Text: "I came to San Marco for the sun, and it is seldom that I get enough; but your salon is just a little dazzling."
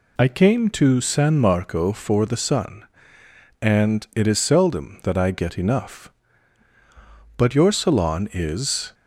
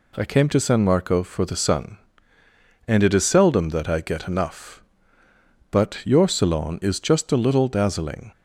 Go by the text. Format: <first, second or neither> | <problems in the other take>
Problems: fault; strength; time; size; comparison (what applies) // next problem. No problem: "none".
second | stops before "just a little dazzling"; at 8.9 s